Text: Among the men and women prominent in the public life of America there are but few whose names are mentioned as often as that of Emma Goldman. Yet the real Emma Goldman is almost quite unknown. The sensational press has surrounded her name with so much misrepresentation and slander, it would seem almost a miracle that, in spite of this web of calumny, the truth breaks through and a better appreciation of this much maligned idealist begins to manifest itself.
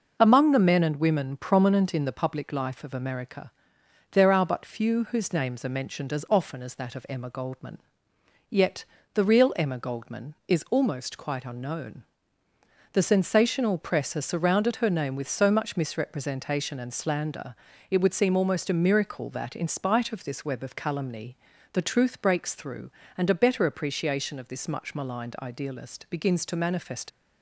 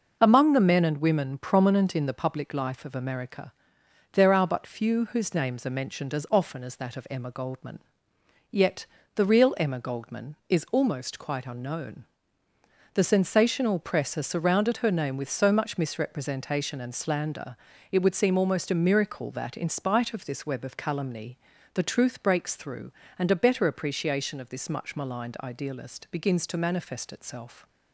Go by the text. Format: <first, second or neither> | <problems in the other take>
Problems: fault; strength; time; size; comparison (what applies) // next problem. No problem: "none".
second | pauses between "America" and "there"; noticeable; at 3.5 s; 0.62 s long; noticeable in the second // pauses between "Yet" and "the"; slight; at 8.8 s; 0.28 s long; slight in the second // stops before "itself"; at 27.0 s